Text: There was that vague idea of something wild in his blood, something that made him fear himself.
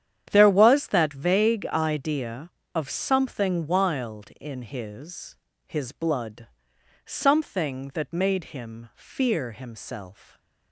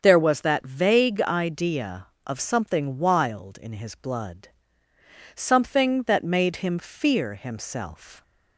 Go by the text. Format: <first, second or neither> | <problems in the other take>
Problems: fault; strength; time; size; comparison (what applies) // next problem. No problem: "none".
second | starts louder than the rest; strong; until 1.3 s; 9.5 dB; strong in the second // says "his" twice; at 5.6 s